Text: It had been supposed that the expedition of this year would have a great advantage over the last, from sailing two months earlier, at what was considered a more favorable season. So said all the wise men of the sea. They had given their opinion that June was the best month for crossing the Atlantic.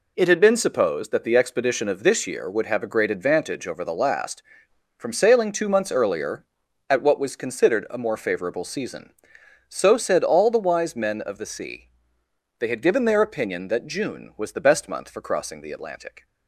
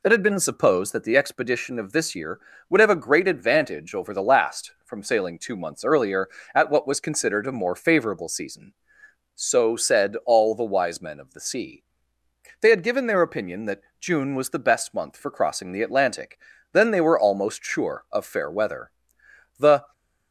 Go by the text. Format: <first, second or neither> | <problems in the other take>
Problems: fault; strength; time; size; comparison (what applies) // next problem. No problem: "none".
first | pauses between "that" and "June"; slight; at 13.8 s; 0.18 s long // goes on to say "Then they were almost sure of fair weather The"; strong; from 16.7 s on; 3.2 s long